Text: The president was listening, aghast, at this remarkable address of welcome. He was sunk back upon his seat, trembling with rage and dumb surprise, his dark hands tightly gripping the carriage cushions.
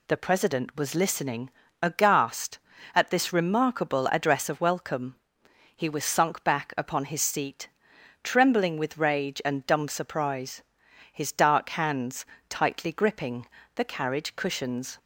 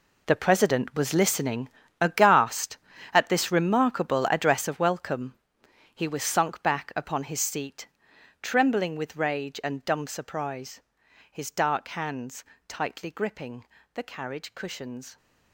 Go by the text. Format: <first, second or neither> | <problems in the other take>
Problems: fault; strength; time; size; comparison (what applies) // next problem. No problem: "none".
first | gets quieter; strong; throughout; 13 dB // pauses between "hands" and "tightly"; slight; at 12.4 s; 0.24 s long; slight in the first // pauses between "gripping" and "the"; slight; at 13.6 s; 0.28 s long; slight in the first